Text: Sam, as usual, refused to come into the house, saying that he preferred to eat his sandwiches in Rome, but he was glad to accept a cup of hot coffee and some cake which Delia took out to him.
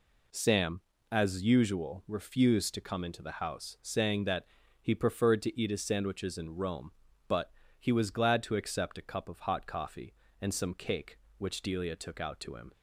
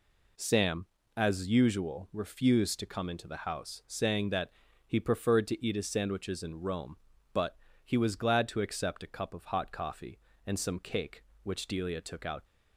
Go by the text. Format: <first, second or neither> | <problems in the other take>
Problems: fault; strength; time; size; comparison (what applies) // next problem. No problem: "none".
first | pauses between "that" and "he"; slight; at 4.5 s; 0.34 s long; slight in the first // pauses between "but" and "he"; slight; at 7.5 s; 0.28 s long; slight in the first // stops before "to him"; at 12.4 s